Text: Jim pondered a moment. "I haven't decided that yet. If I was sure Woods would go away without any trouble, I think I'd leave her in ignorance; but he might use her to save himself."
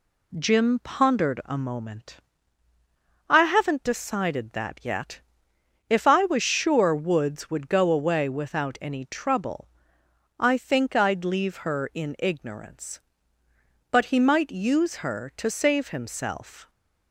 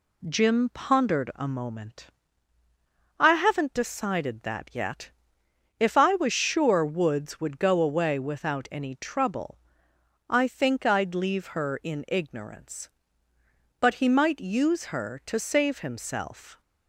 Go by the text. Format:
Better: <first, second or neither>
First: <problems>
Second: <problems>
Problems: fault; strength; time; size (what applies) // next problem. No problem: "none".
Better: neither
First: none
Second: none